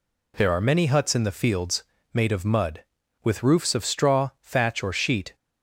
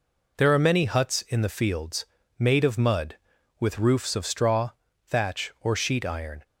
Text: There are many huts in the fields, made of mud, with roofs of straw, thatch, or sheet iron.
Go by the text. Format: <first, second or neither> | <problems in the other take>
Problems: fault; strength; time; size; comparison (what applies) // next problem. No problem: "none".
second | stops before "iron"; at 5.3 s